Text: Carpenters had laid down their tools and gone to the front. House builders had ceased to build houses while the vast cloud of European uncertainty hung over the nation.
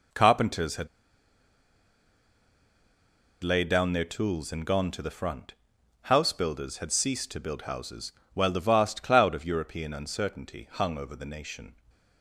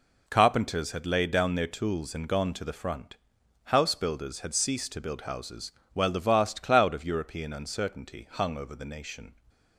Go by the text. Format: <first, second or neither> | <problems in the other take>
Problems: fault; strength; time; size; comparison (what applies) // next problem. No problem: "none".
second | pauses between "had" and "laid"; strong; at 0.8 s; 2.5 s long // pauses between "houses" and "while"; slight; at 8.1 s; 0.22 s long; slight in the second